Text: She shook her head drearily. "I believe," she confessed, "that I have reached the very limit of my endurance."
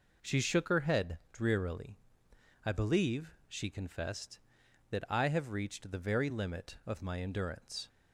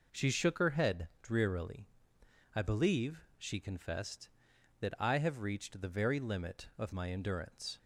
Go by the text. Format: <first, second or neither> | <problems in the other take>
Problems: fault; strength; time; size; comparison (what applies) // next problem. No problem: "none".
neither | none